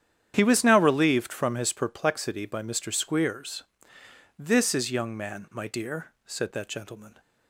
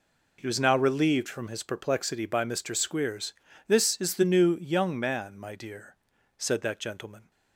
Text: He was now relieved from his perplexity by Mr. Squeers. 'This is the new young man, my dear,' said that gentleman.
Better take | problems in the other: second | starts louder than the rest; strong; until 1.3 s; 9.5 dB // skips "the new"; at 4.9 s

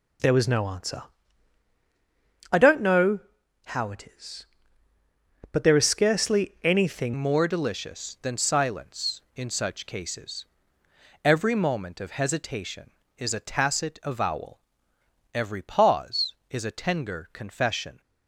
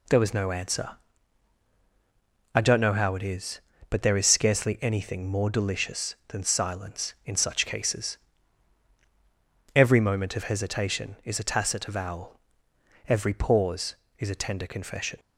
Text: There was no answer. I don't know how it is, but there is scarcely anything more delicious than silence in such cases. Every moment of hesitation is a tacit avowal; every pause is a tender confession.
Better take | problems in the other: second | pauses between "know" and "how"; at 3.2 s; 0.44 s long // changes voice at "more"; from 7.1 s on; 10.9 s long

